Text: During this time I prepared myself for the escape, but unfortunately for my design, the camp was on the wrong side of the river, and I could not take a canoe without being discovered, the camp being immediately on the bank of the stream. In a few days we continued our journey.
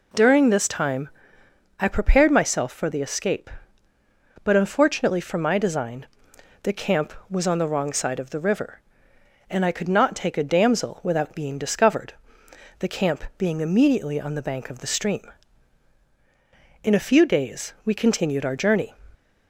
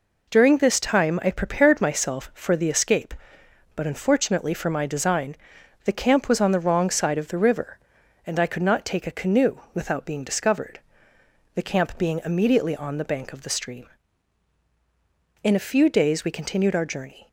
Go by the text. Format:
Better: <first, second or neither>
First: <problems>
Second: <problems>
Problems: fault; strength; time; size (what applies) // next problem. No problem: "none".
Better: second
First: pauses between "time" and "I"; noticeable; at 1.0 s; 0.72 s long // says "damsel" for "canoe"; at 10.4 s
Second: none